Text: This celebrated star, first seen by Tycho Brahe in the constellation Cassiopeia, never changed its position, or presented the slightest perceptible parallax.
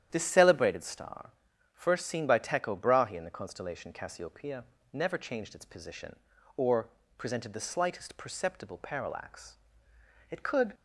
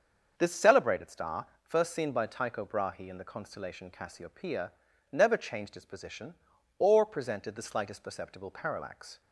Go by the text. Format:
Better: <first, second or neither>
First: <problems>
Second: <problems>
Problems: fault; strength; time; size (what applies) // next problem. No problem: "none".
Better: second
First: starts louder than the rest; strong; until 1.1 s; 10 dB // pauses between "or" and "presented"; slight; at 6.8 s; 0.28 s long // goes on to say "It could"; slight; from 10.2 s on; 0.44 s long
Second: starts louder than the rest; until 1.3 s; 6.5 dB